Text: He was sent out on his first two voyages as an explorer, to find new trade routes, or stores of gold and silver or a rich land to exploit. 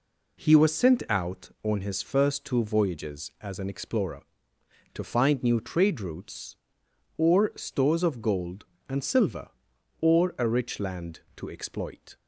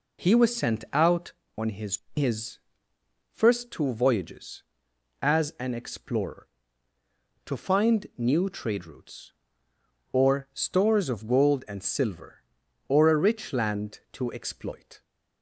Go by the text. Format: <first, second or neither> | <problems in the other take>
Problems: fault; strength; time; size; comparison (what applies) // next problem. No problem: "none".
first | says "his" twice; at 2.1 s